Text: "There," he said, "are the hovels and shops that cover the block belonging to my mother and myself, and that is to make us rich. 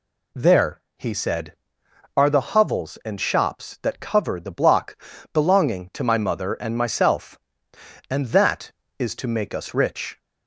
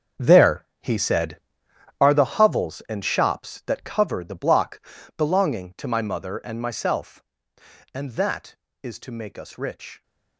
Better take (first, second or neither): first